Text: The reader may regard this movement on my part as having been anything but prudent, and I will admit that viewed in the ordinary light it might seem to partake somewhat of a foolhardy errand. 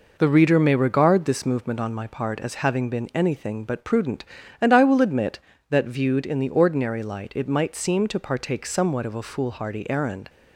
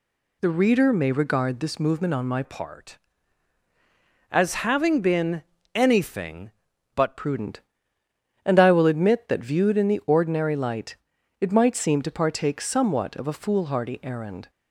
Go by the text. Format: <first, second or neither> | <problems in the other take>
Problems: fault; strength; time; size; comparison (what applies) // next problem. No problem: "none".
first | changes voice from "part" to "but"; from 2.4 to 7.1 s; 4.7 s long // pauses between "been" and "anything"; slight; at 5.4 s; 0.32 s long // pauses between "light" and "it"; at 10.9 s; 0.44 s long